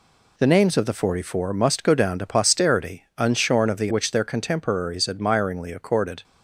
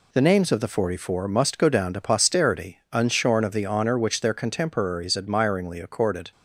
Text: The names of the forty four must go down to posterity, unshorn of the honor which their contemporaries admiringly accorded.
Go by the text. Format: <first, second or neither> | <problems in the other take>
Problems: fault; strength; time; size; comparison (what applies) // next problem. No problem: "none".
second | skips "honor"; at 3.8 s